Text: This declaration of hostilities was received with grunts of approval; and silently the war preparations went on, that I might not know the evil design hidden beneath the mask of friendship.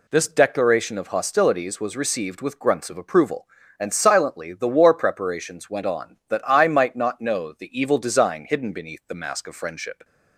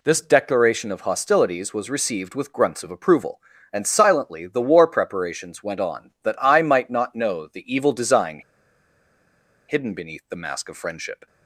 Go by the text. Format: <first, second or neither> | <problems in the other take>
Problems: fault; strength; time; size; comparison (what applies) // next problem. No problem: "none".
first | pauses between "design" and "hidden"; strong; at 8.4 s; 1.2 s long